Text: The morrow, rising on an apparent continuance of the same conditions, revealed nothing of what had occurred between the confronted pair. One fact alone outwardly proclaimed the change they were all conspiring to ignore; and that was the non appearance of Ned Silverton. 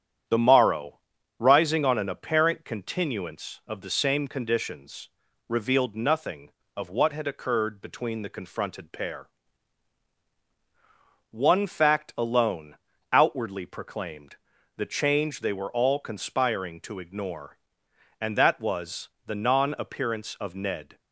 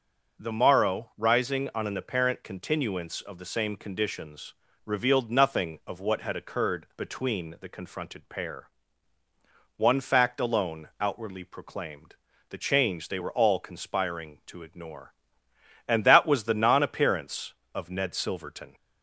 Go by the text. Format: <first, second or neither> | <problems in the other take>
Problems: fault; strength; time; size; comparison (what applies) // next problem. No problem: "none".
second | starts louder than the rest; strong; until 1.6 s; 9.5 dB; also in the second // pauses between "alone" and "outwardly"; slight; at 12.7 s; 0.34 s long // pauses between "proclaimed" and "the"; at 14.3 s; 0.40 s long; slight in the second // pauses between "was" and "the"; slight; at 19.0 s; 0.16 s long // stops before "Silverton"; at 20.9 s